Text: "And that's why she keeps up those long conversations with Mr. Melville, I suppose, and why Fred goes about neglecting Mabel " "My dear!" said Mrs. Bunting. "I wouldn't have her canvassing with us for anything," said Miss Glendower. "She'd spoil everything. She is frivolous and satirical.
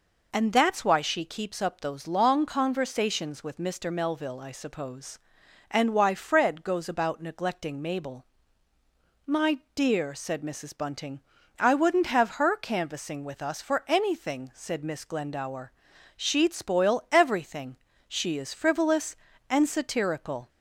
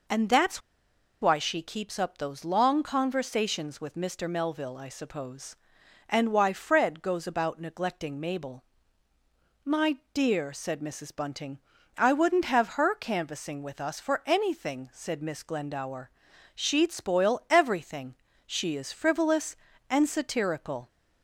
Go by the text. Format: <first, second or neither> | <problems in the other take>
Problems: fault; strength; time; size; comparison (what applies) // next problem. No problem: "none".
first | pauses between "that's" and "why"; noticeable; at 0.6 s; 0.60 s long // pauses between "My" and "dear"; slight; at 9.9 s; 0.16 s long; slight in the first